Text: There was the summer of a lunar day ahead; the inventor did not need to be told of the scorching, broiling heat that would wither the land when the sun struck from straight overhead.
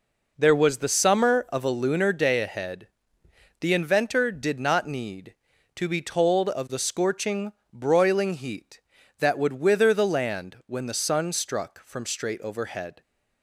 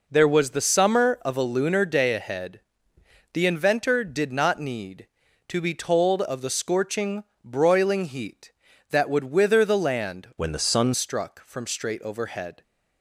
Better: first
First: none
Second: changes voice from "when" to "sun"; from 10.3 to 10.9 s; 0.6 s long

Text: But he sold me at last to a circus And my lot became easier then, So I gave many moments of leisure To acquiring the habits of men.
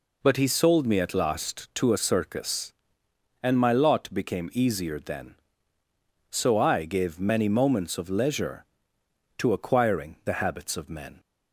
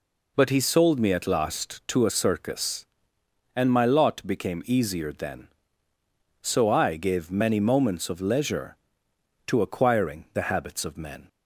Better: neither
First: none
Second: none

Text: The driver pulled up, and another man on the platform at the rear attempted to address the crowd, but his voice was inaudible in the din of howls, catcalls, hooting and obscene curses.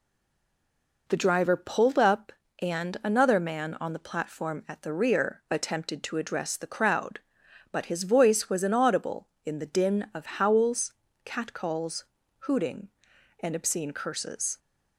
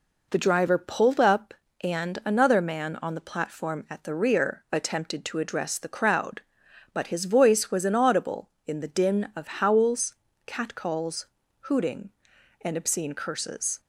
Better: second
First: stays silent before the first word; until 1.0 s; 1.0 s long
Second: none

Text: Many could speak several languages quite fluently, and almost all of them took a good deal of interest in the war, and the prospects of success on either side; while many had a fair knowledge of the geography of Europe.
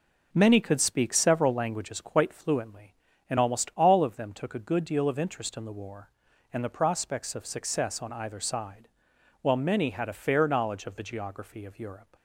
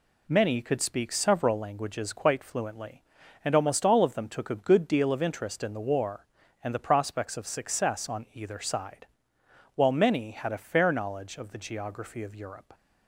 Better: neither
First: none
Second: none

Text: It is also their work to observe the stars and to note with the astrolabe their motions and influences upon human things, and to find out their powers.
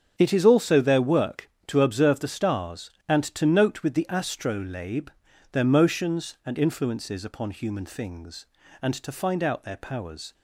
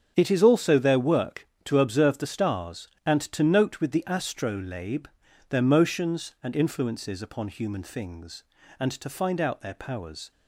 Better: neither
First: starts louder than the rest; strong; until 1.1 s; 7.5 dB // pauses between "astrolabe" and "their"; at 5.0 s; 0.42 s long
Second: starts louder than the rest; strong; until 1.1 s; 7.5 dB // pauses between "astrolabe" and "their"; at 5.0 s; 0.42 s long

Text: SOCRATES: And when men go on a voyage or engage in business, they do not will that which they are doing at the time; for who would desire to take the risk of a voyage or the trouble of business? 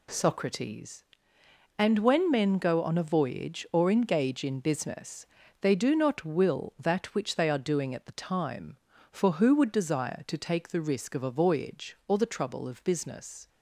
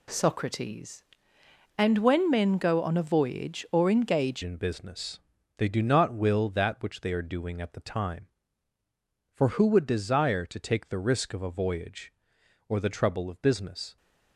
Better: first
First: none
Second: changes voice at "in"; from 4.4 s on; 9.5 s long

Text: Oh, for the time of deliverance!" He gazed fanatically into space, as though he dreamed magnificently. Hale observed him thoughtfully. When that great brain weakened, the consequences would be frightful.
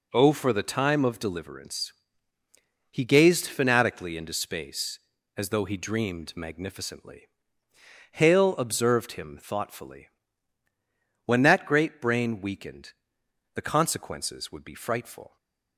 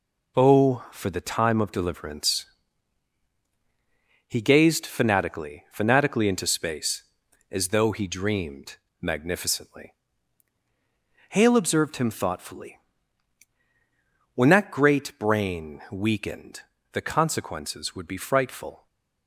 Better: first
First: stays silent after the last word; slight; from 15.2 s on; 0.5 s long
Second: says "fanatically" twice; at 5.7 s // pauses between "dreamed" and "magnificently"; slight; at 8.7 s; 0.24 s long // stays silent after the last word; slight; from 18.7 s on; 0.5 s long

